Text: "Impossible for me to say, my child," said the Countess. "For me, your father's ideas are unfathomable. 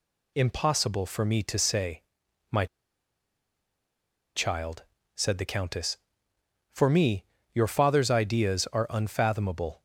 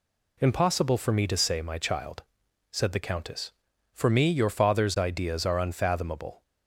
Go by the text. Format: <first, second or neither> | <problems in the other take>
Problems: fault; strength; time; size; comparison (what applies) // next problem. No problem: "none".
second | pauses between "my" and "child"; strong; at 2.6 s; 1.7 s long